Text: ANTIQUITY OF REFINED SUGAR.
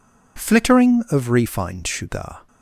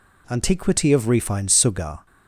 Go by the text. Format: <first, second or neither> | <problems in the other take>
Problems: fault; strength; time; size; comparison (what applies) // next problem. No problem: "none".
second | says "Flittering" for "ANTIQUITY"; at 0.3 s